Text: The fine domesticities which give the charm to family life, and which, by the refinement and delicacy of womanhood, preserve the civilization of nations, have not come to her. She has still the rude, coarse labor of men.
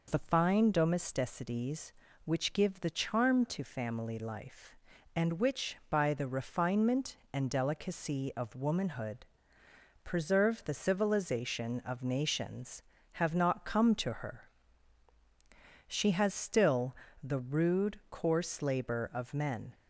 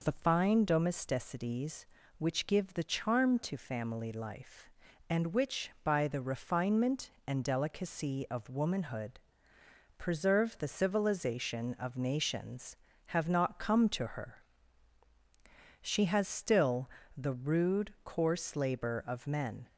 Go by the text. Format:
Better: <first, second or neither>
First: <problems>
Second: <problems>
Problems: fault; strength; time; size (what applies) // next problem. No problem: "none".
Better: neither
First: pauses between "still" and "the"; slight; at 16.9 s; 0.26 s long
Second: pauses between "still" and "the"; slight; at 16.9 s; 0.26 s long